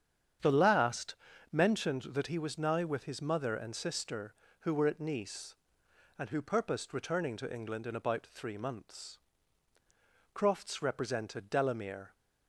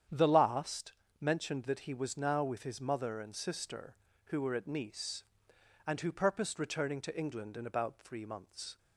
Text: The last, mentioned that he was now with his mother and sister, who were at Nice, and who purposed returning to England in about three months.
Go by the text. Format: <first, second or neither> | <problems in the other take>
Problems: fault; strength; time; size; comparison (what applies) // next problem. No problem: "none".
second | starts louder than the rest; strong; until 1.7 s; 8.5 dB; strong in the second // goes on to say "Crofts represented Delamere"; strong; from 10.3 s on; 1.8 s long